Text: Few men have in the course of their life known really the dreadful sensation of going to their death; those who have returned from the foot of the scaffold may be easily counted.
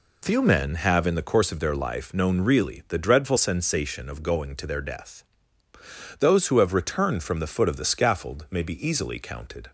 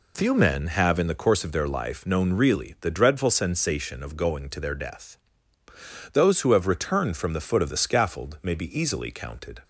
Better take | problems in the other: neither | none

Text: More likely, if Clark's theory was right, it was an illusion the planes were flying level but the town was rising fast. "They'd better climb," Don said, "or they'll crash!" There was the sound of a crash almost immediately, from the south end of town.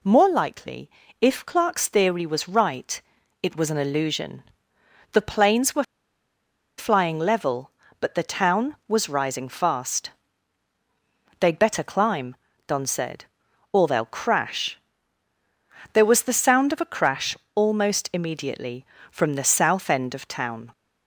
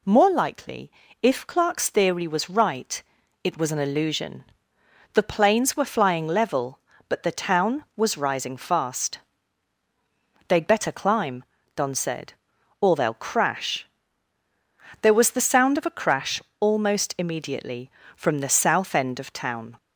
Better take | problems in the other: second | pauses between "illusion" and "the"; noticeable; at 4.4 s; 0.68 s long; noticeable in the second // pauses between "were" and "flying"; noticeable; at 5.8 s; 0.94 s long // pauses between "crash" and "almost"; slight; at 17.3 s; 0.20 s long; slight in the second

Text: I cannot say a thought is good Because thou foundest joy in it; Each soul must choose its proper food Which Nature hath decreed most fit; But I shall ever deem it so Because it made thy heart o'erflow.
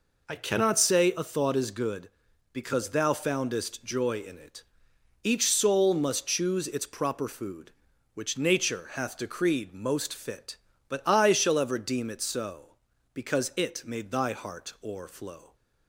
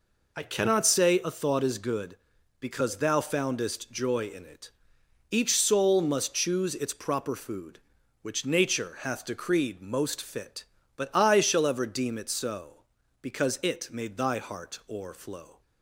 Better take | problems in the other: neither | none

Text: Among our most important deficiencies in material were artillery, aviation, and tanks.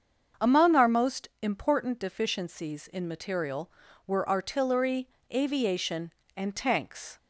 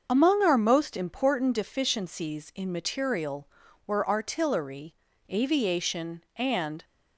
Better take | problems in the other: first | starts louder than the rest; until 1.0 s; 6.5 dB; also in the first // stops before "tanks"; at 6.8 s

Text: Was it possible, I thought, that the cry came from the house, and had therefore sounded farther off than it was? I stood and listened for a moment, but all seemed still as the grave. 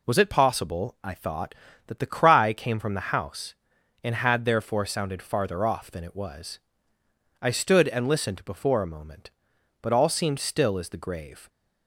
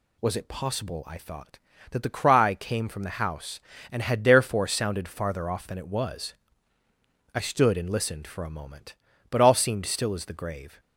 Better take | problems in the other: second | says "before" for "for"; at 8.4 s

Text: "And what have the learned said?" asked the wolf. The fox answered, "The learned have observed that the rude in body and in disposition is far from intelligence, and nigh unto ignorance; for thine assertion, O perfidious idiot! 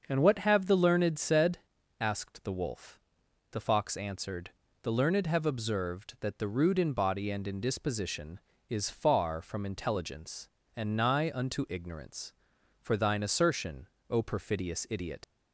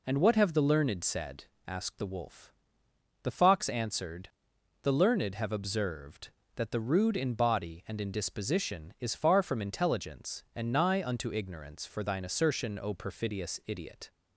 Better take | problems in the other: second | starts louder than the rest; until 1.0 s; 6.5 dB // leaves "idiot" unfinished; at 15.2 s; 100 ms

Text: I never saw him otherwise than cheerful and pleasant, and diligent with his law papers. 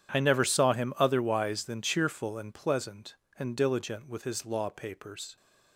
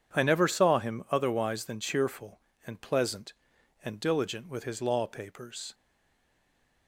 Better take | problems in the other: first | stays silent after the last word; from 5.7 s on; 1.1 s long

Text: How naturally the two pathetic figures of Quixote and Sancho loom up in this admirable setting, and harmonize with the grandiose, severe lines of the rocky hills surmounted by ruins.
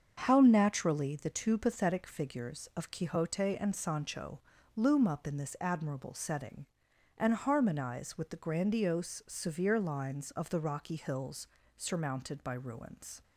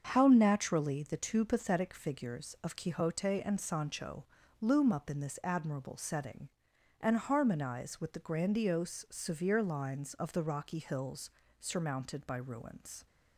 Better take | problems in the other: neither | starts louder than the rest; the same in both // pauses between "Sancho" and "loom"; the same in both // pauses between "hills" and "surmounted"; slight; the same in both

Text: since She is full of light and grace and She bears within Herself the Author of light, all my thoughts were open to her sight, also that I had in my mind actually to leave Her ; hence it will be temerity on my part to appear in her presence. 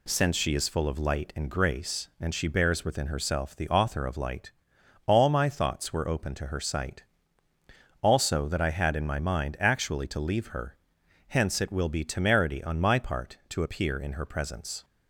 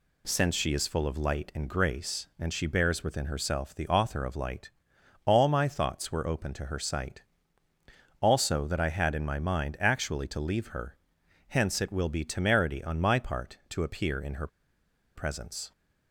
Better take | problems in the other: first | pauses between "her" and "presence"; noticeable; at 14.4 s; 0.67 s long

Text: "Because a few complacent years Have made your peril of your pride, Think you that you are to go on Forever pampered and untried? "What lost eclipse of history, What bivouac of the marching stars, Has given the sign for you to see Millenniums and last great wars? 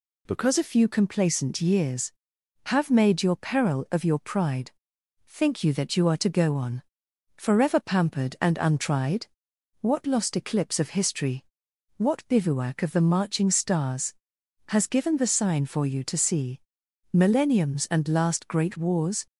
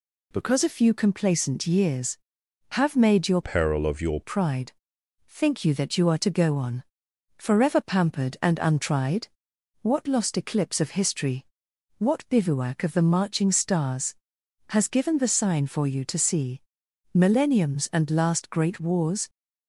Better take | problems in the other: first | changes voice from "peril" to "your"; from 3.4 to 4.2 s; 0.8 s long // pauses between "on" and "Forever"; noticeable; at 6.8 s; 0.54 s long; noticeable in the first // pauses between "see" and "Millenniums"; noticeable; at 16.6 s; 0.52 s long; noticeable in the first

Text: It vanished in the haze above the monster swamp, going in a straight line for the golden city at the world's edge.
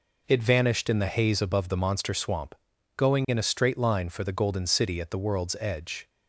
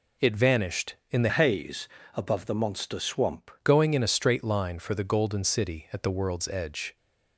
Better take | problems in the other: first | changes voice from "haze" to "swamp"; from 1.2 to 3.5 s; 2.3 s long // pauses between "haze" and "above"; slight; at 1.8 s; 0.26 s long

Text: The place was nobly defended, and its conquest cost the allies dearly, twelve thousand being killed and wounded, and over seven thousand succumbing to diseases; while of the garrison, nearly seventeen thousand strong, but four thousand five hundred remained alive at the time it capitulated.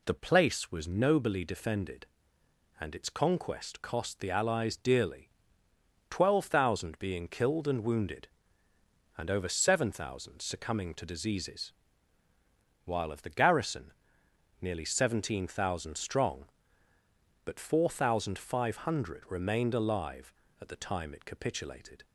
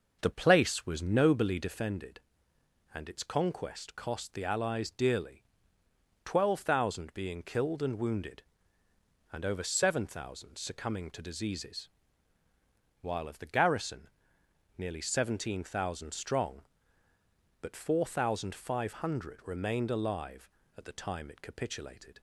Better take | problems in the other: first | starts louder than the rest; noticeable; until 1.8 s; 6 dB

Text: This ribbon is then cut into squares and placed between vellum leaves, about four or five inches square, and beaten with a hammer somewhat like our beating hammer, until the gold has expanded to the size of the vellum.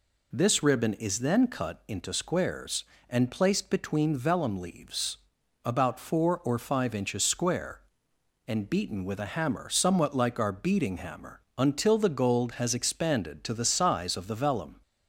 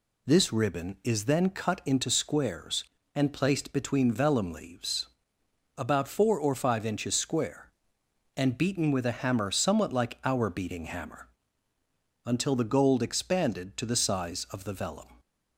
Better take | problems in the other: first | skips "has"; at 13.0 s

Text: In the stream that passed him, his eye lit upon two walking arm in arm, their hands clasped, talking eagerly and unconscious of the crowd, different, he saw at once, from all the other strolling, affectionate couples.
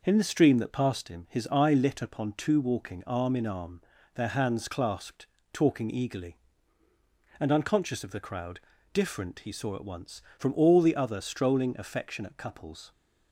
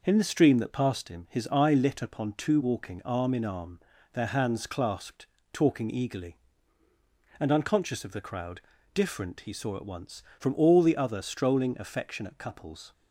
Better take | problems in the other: neither | none

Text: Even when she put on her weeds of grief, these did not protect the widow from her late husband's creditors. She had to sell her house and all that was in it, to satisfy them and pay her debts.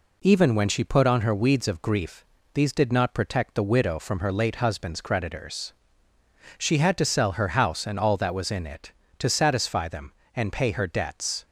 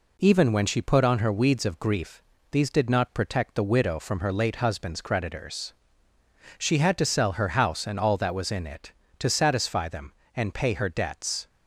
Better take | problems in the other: neither | none

